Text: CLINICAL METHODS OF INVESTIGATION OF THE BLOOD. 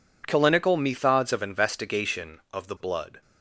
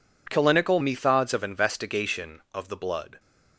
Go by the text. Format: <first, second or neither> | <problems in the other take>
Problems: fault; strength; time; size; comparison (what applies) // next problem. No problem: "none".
neither | none